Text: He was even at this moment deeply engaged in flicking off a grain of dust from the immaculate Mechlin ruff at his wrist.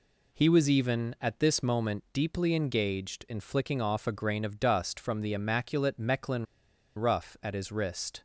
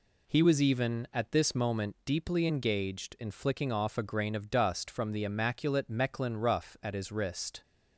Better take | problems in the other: second | pauses between "Mechlin" and "ruff"; noticeable; at 6.4 s; 0.55 s long

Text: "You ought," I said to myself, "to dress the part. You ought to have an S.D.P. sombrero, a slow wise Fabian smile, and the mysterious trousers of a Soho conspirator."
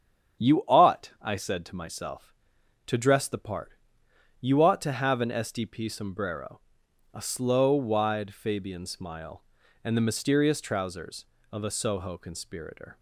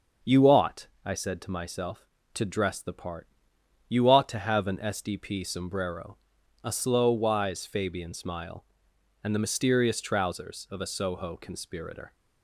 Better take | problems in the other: second | starts louder than the rest; strong; until 1.5 s; 8.5 dB; also in the second // says "wide" for "wise"; at 7.7 s

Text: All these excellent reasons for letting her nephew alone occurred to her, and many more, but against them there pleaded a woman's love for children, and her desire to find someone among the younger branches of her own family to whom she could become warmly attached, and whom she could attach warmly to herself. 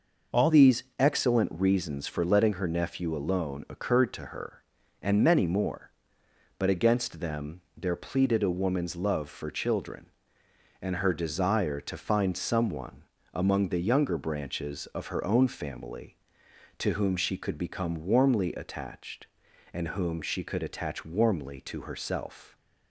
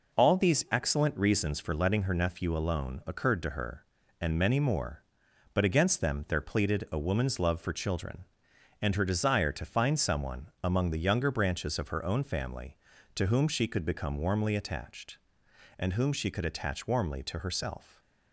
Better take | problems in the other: second | changes voice at "these"; from 0.4 s on; 22.1 s long // pauses between "someone" and "among"; slight; at 13.0 s; 0.30 s long; slight in the second

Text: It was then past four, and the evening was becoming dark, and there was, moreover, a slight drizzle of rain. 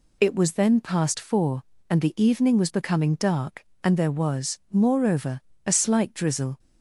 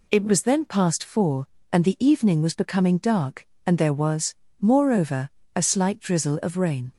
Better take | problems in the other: second | stops before "of rain"; at 6.5 s

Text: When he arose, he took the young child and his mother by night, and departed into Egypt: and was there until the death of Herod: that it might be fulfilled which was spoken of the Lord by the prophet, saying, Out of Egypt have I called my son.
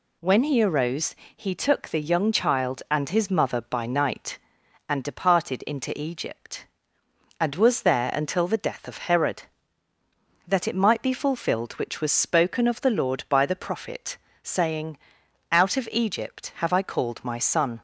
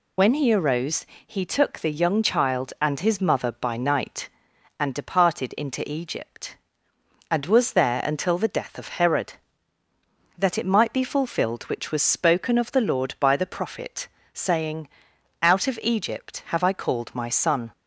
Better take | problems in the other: first | loses the start of "When"; at 0.1 s; 65 ms

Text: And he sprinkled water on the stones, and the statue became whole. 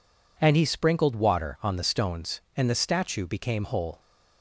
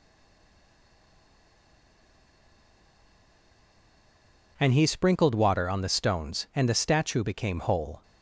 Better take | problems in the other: first | stays silent before the first word; strong; until 4.5 s; 4.5 s long

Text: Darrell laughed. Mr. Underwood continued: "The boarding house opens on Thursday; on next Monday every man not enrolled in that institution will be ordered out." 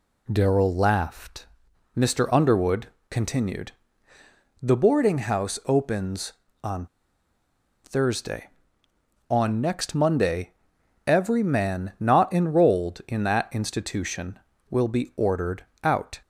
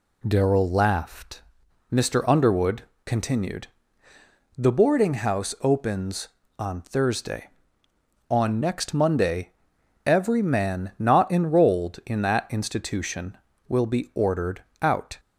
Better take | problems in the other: second | pauses between "Underwood" and "continued"; slight; at 2.8 s; 0.22 s long; slight in the second // pauses between "on" and "Thursday"; noticeable; at 6.8 s; 0.97 s long // pauses between "Monday" and "every"; noticeable; at 10.5 s; 0.52 s long; noticeable in the second // pauses between "ordered" and "out"; slight; at 15.6 s; 0.20 s long; slight in the second

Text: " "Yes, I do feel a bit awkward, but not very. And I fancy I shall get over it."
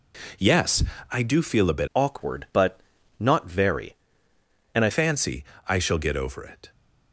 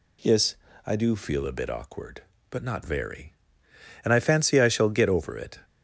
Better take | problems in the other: second | changes voice from "awkward" to "I"; from 1.9 to 4.8 s; 2.9 s long // pauses between "but" and "not"; slight; at 2.8 s; 0.36 s long // pauses between "fancy" and "I"; slight; at 5.4 s; 0.22 s long

